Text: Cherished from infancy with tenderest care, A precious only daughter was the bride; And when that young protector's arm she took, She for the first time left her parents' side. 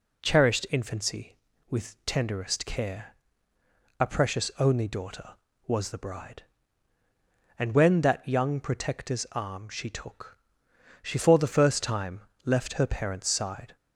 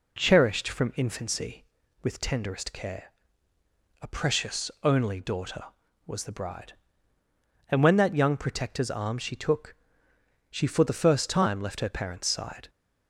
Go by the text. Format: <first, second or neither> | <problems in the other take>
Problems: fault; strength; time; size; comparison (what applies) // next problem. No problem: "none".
second | skips "from"; at 0.6 s // pauses between "time" and "left"; slight; at 12.2 s; 0.22 s long